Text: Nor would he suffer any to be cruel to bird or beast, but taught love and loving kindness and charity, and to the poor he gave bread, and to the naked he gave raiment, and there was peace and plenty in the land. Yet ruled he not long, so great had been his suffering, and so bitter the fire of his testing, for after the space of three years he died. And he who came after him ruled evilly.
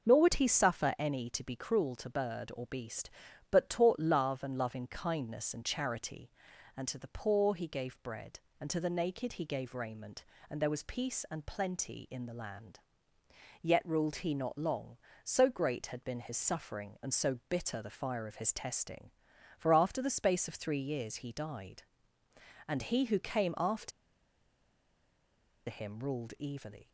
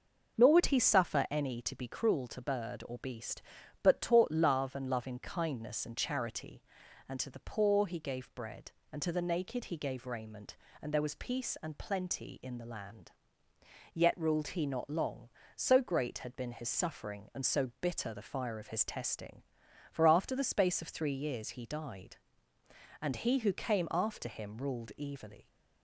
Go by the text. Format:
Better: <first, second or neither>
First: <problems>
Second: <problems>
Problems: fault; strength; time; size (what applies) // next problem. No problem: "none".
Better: second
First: starts louder than the rest; until 1.1 s; 6.5 dB // pauses between "after" and "him"; strong; at 23.9 s; 1.7 s long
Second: starts louder than the rest; until 1.4 s; 6.5 dB